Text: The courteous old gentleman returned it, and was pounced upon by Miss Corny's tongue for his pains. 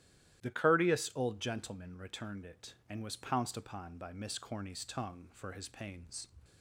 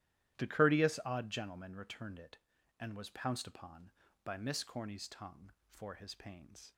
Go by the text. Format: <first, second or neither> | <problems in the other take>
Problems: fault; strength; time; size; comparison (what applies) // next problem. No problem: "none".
first | starts louder than the rest; strong; until 1.4 s; 13 dB; strong in the first // says "odd" for "old"; at 1.0 s